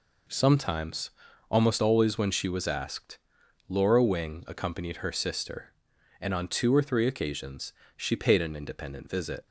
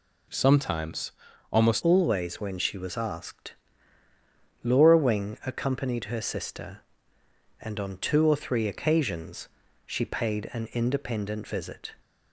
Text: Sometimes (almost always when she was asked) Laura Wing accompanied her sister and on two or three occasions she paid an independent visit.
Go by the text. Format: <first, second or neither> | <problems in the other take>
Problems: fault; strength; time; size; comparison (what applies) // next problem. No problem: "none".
first | changes voice at "always"; from 1.8 s on; 10.1 s long // pauses between "occasions" and "she"; slight; at 9.4 s; 0.36 s long; slight in the first